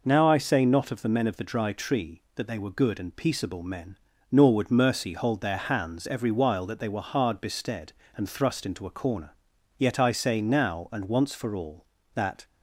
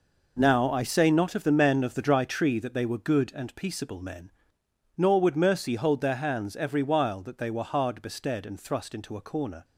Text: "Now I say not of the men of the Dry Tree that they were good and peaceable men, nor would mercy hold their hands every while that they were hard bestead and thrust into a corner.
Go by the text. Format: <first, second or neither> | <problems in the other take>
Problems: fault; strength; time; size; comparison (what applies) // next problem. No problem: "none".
second | goes on to say "Yet I say now and once for all that"; strong; from 9.7 s on; 2.6 s long